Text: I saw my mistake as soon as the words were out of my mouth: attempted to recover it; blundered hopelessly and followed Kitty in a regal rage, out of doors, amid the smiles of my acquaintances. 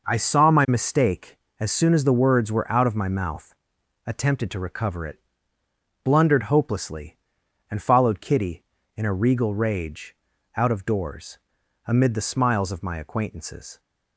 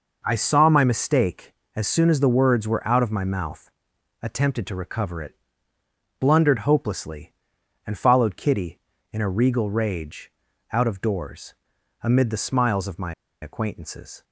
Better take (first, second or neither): first